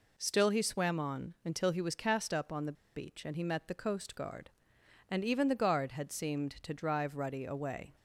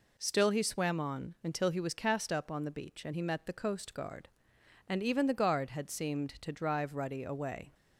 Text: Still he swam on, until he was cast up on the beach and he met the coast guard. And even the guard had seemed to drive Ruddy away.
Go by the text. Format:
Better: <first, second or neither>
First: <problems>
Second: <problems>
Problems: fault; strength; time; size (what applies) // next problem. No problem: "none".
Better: second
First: pauses between "the" and "beach"; slight; at 2.7 s; 0.22 s long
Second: none